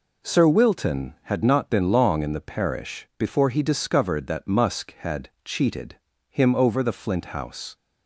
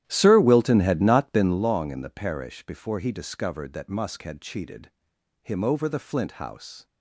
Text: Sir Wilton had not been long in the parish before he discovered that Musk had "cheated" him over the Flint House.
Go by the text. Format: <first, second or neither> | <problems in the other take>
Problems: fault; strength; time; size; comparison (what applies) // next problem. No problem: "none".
first | starts louder than the rest; strong; until 1.7 s; 12 dB // pauses between "cheated" and "him"; noticeable; at 4.9 s; 0.50 s long; slight in the first